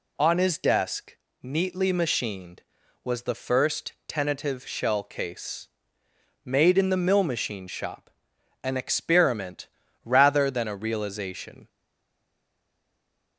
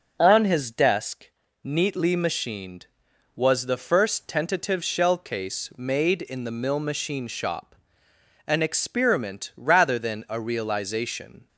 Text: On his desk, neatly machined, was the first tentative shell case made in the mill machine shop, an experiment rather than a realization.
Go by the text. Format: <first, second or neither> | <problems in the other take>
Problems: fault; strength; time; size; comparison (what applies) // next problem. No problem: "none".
second | pauses between "first" and "tentative"; slight; at 3.9 s; 0.16 s long // pauses between "case" and "made"; noticeable; at 5.6 s; 0.76 s long // pauses between "experiment" and "rather"; slight; at 9.6 s; 0.36 s long // stays silent after the last word; noticeable; from 11.6 s on; 1.7 s long